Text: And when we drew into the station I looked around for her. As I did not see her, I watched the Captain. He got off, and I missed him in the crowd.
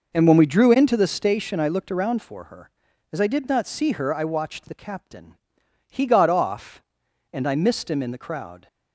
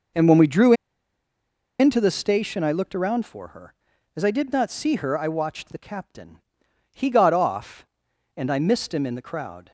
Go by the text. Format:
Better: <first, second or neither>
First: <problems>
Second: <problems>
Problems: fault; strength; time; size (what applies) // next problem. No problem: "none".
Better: first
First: none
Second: pauses between "drew" and "into"; at 0.7 s; 1.0 s long